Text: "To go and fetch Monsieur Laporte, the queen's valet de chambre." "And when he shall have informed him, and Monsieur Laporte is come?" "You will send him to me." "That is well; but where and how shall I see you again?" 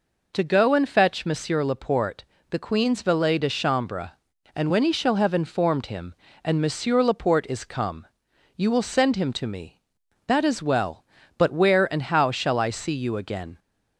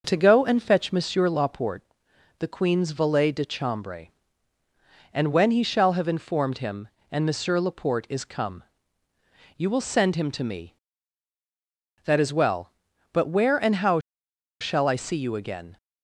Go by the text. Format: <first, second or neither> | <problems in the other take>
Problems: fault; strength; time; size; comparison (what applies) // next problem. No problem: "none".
first | starts louder than the rest; noticeable; until 1.0 s; 6 dB // pauses between "how" and "shall"; noticeable; at 13.9 s; 0.61 s long